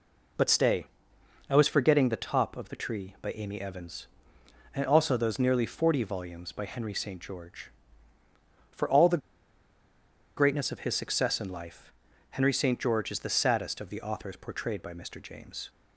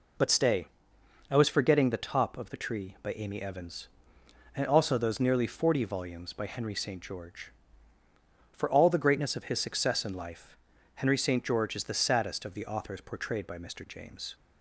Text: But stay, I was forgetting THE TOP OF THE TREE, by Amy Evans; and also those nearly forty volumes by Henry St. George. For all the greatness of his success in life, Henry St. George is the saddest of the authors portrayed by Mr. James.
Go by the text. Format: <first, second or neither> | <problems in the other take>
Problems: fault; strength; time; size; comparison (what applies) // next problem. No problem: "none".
second | pauses between "the" and "greatness"; at 9.2 s; 1.1 s long